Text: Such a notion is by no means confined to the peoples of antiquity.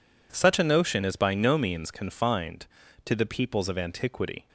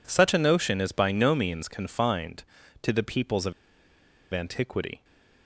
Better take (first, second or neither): first